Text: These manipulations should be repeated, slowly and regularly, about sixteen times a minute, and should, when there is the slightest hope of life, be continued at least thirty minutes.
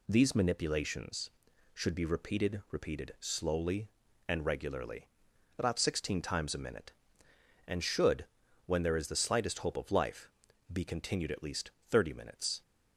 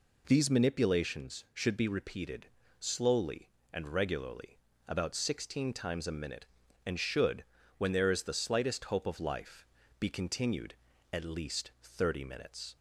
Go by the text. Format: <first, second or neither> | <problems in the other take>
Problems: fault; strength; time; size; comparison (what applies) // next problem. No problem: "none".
second | says "repeated" twice; at 2.6 s // pauses between "least" and "thirty"; slight; at 11.7 s; 0.18 s long